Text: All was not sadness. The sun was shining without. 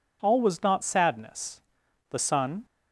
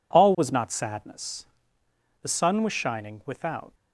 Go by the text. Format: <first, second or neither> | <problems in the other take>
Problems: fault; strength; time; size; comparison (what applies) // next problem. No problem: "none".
second | stops before "was shining without"; at 2.6 s